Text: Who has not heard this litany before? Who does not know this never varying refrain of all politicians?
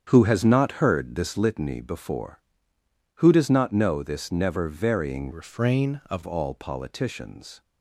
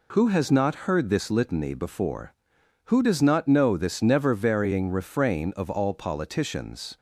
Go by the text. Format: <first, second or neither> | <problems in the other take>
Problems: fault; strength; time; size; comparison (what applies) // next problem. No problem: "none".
second | starts louder than the rest; strong; until 1.0 s; 8 dB // changes voice from "refrain" to "of"; from 5.3 to 6.2 s; 0.9 s long